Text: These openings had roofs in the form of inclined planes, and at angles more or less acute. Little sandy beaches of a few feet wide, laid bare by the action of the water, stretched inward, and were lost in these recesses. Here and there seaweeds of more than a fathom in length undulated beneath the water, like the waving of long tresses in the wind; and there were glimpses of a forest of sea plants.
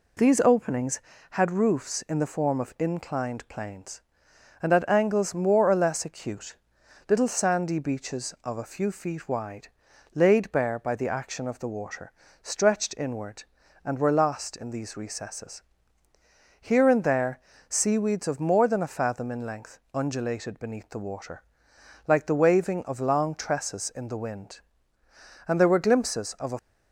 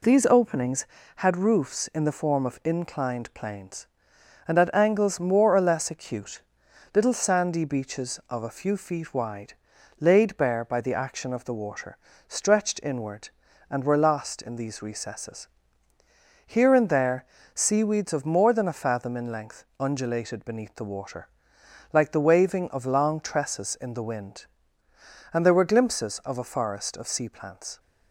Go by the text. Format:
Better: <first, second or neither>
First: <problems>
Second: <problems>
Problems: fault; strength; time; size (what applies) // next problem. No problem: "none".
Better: second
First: pauses between "there" and "seaweeds"; slight; at 17.3 s; 0.30 s long // pauses between "length" and "undulated"; slight; at 19.7 s; 0.16 s long // stops before "forest of sea plants"; at 26.5 s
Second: pauses between "there" and "seaweeds"; slight; at 17.2 s; 0.30 s long // pauses between "length" and "undulated"; slight; at 19.6 s; 0.16 s long